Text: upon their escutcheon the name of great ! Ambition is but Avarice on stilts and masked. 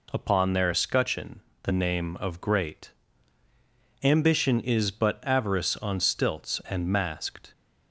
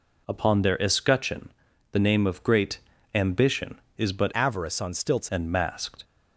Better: first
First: pauses between "escutcheon" and "the"; slight; at 1.4 s; 0.22 s long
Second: pauses between "escutcheon" and "the"; at 1.4 s; 0.42 s long // changes voice from "Avarice" to "stilts"; from 4.3 to 5.2 s; 0.9 s long

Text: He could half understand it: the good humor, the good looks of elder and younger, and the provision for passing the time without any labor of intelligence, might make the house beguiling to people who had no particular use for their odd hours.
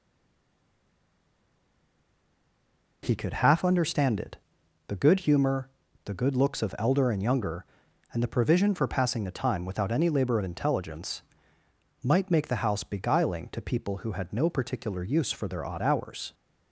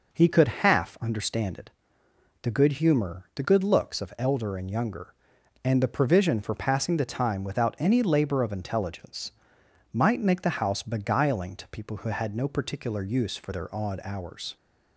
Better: second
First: stays silent before the first word; strong; until 3.0 s; 3.0 s long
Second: none

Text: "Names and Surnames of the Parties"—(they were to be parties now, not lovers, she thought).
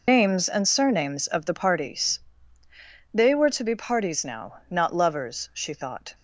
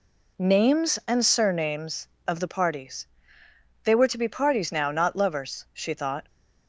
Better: second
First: loses the start of "Names"; at 0.0 s; 95 ms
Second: none

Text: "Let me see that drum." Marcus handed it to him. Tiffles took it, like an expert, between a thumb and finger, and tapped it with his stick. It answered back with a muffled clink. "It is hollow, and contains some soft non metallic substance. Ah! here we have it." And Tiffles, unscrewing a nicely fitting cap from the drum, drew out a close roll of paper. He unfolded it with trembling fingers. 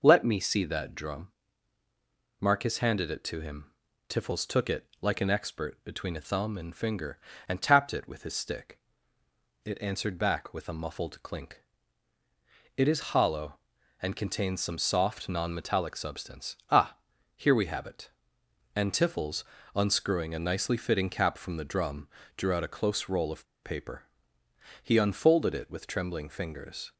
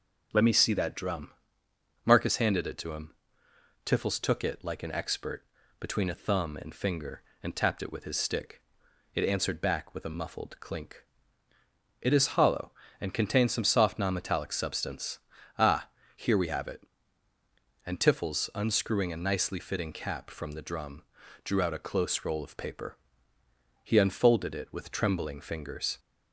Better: second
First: pauses between "of" and "paper"; slight; at 23.4 s; 0.19 s long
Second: none

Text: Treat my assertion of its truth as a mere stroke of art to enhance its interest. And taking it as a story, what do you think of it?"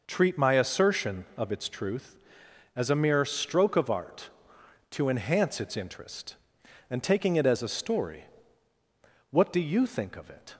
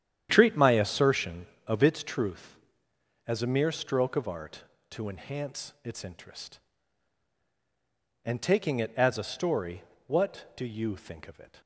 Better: first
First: none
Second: starts louder than the rest; strong; until 2.1 s; 10 dB

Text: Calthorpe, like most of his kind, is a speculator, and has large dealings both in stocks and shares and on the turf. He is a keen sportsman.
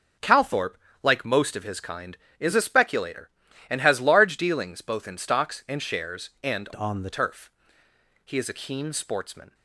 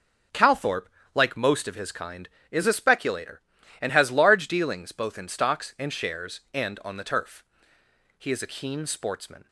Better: second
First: changes voice from "on" to "the"; from 6.7 to 7.1 s; 0.4 s long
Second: none

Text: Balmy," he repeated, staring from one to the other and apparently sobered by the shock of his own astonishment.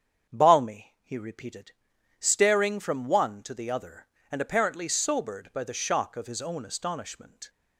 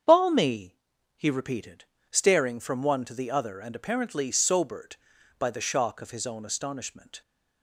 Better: neither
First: starts louder than the rest; strong; until 1.3 s; 8 dB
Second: starts louder than the rest; strong; until 1.4 s; 7.5 dB

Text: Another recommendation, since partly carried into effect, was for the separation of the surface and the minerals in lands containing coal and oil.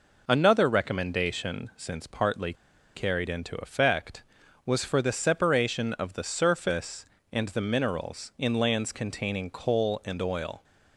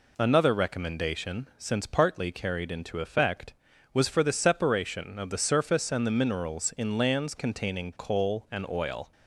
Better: second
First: pauses between "partly" and "carried"; at 2.5 s; 0.40 s long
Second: none

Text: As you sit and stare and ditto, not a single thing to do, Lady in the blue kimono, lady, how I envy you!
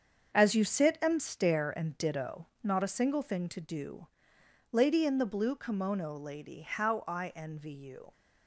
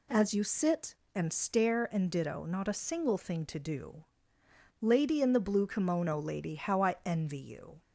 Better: second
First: gets quieter; strong; throughout; 8.5 dB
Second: none

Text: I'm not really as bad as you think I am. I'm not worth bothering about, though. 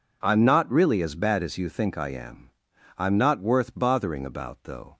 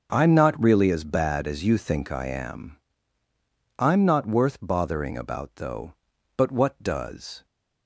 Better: first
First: none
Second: starts louder than the rest; until 1.1 s; 6.5 dB // goes on to say "But what does"; noticeable; from 6.3 s on; 1.1 s long

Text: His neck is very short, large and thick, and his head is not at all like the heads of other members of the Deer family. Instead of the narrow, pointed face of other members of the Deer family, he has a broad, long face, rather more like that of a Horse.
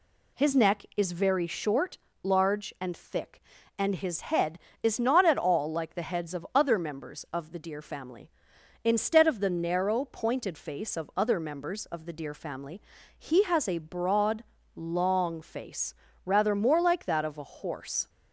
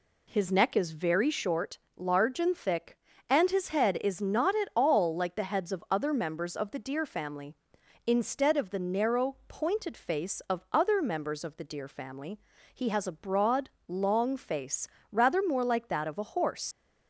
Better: first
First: none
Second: leaves "Horse" unfinished; at 16.7 s; 75 ms

